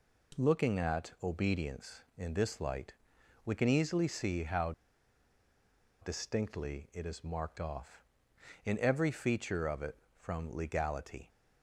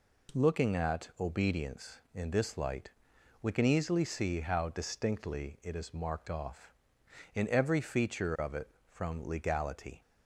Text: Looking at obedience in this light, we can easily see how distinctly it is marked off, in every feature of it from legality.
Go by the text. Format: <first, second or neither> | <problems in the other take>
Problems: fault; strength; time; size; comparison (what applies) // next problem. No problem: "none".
second | pauses between "how" and "distinctly"; strong; at 4.7 s; 1.3 s long